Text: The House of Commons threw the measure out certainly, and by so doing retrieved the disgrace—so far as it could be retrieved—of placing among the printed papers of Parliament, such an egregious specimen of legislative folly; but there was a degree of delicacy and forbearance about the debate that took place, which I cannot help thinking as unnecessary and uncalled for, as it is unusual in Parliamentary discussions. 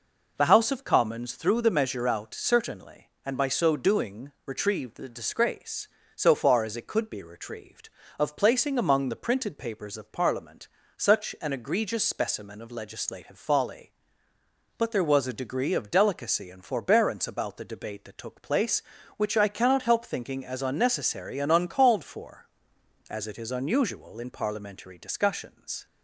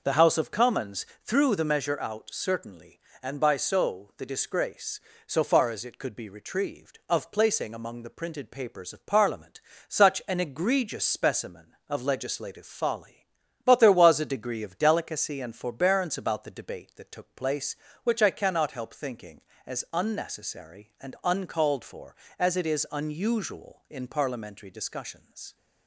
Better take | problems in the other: first | starts louder than the rest; until 1.0 s; 6 dB // pauses between "Commons" and "threw"; slight; at 1.0 s; 0.18 s long // skips "doing retrieved"; at 4.1 s

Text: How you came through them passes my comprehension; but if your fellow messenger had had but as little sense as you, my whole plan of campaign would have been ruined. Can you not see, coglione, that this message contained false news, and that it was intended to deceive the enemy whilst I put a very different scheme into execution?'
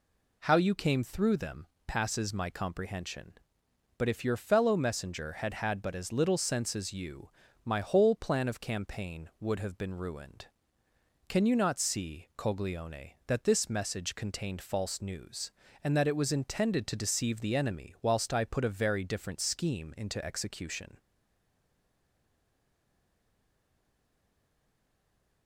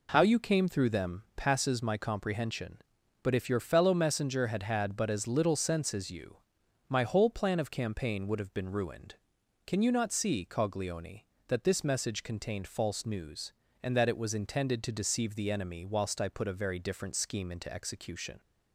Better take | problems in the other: second | pauses between "them" and "passes"; slight; at 1.6 s; 0.22 s long // stays silent after the last word; strong; from 20.9 s on; 4.5 s long

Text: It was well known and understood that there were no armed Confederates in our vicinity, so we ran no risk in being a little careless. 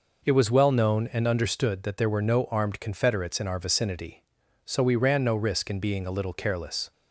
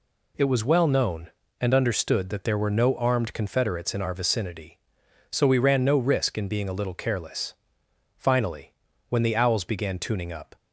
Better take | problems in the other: first | goes on to say "Finally when the owls began tuning up"; strong; from 8.1 s on; 2.3 s long

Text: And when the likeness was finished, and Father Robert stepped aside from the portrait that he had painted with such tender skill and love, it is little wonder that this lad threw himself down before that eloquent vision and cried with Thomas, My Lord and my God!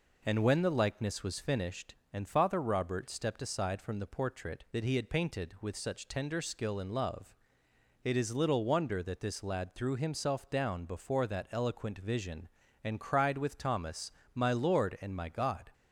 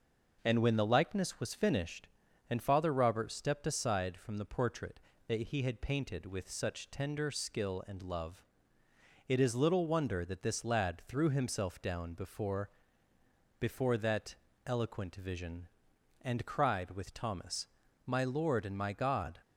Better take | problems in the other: first | says "before" twice; at 13.5 s // pauses between "that" and "eloquent"; slight; at 14.3 s; 0.30 s long

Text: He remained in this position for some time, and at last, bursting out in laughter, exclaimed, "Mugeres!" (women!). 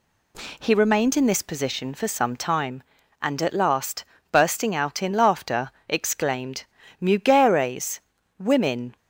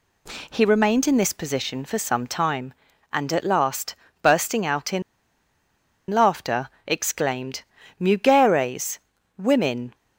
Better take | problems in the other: first | pauses between "in" and "laughter"; at 5.0 s; 1.0 s long

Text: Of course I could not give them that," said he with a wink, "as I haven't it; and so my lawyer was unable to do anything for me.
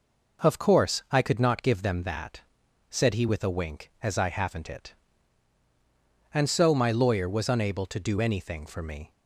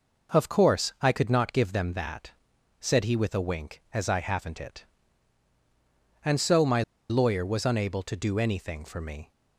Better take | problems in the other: first | pauses between "my" and "lawyer"; slight; at 6.8 s; 0.27 s long

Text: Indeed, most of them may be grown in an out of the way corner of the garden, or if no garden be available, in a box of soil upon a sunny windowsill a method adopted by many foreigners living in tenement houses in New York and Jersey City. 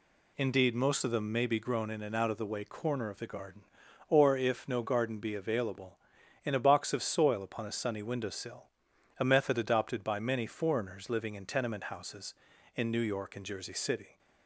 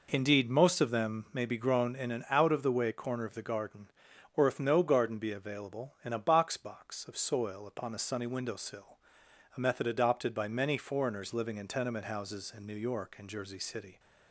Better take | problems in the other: first | says "box" twice; at 6.5 s // pauses between "windowsill" and "a"; noticeable; at 8.9 s; 0.62 s long; noticeable in the first

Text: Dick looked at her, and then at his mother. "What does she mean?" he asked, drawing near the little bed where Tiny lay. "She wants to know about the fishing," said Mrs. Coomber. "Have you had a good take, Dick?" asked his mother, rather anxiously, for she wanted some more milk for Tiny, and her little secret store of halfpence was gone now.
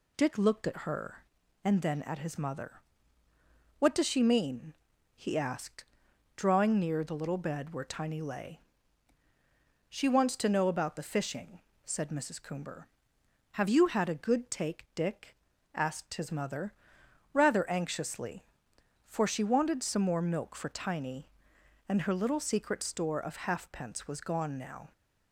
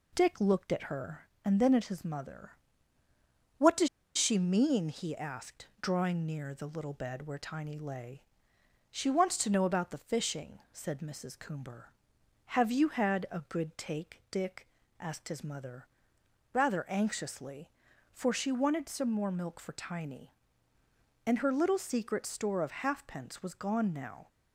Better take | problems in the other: first | pauses between "does" and "she"; slight; at 3.8 s; 0.28 s long

